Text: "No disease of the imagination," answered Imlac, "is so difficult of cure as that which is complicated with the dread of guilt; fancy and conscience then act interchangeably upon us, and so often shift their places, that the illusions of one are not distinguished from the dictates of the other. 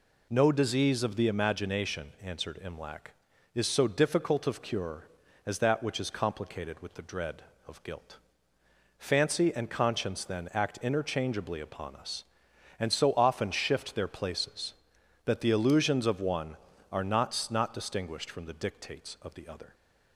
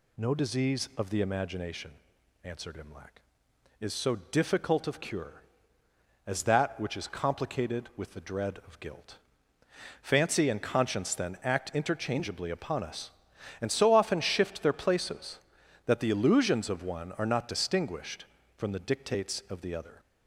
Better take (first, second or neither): second